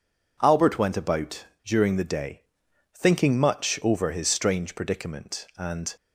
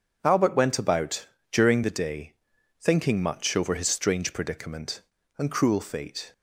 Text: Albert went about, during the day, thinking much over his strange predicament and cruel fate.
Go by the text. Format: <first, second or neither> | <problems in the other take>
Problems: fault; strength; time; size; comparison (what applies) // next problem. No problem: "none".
second | stops before "cruel fate"; at 5.9 s